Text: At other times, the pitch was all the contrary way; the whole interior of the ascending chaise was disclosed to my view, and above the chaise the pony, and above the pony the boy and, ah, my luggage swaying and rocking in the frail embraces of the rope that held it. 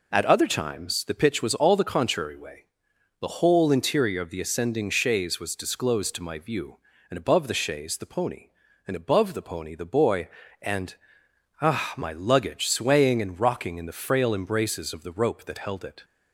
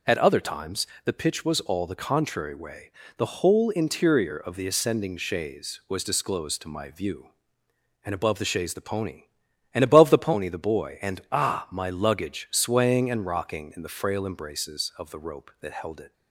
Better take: neither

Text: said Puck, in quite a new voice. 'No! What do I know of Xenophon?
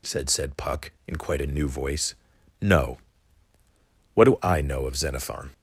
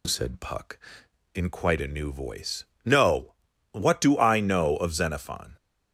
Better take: second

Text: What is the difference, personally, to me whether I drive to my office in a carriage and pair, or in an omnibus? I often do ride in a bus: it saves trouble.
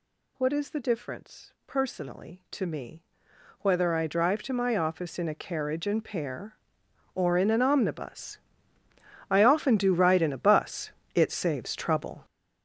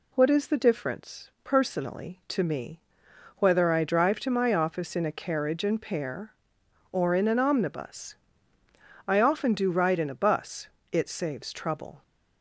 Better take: second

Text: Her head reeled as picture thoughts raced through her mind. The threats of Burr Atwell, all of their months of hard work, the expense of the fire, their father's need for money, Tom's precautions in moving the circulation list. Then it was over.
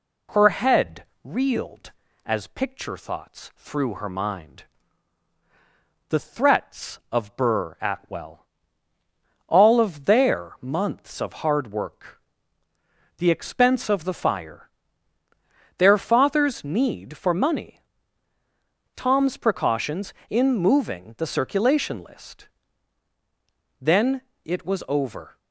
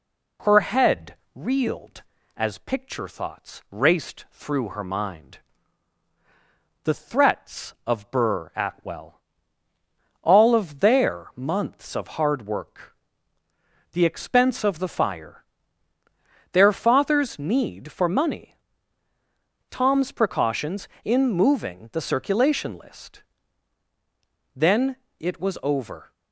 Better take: second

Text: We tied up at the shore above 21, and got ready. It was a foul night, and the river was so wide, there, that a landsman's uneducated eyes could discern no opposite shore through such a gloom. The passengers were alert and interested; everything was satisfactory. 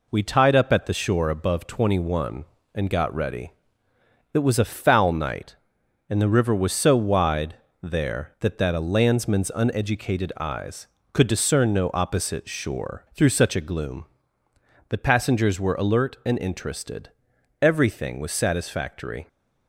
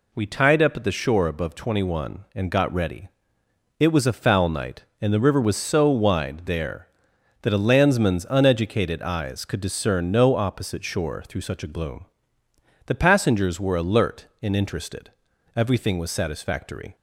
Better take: second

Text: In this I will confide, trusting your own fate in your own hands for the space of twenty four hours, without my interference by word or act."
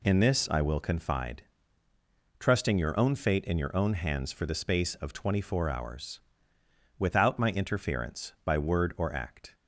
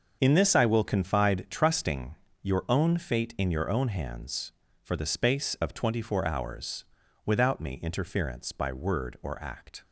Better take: first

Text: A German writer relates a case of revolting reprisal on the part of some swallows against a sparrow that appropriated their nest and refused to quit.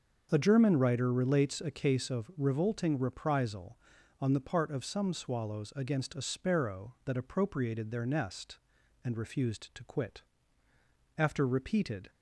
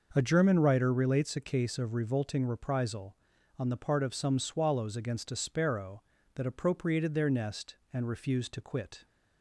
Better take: second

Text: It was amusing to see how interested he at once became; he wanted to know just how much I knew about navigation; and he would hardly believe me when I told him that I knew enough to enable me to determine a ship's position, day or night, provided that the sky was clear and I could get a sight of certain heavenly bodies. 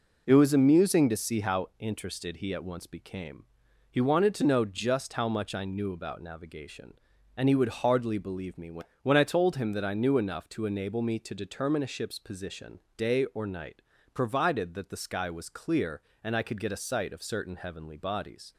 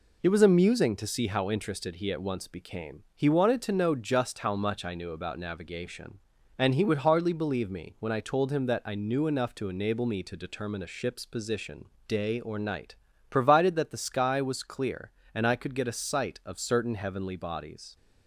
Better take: second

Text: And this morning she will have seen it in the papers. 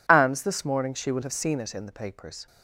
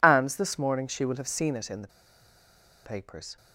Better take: first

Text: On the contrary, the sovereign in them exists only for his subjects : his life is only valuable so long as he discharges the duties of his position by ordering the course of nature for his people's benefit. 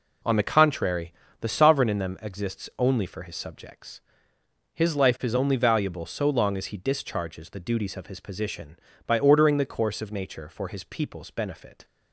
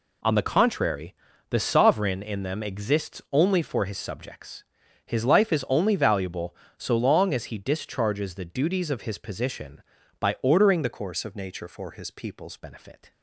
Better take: first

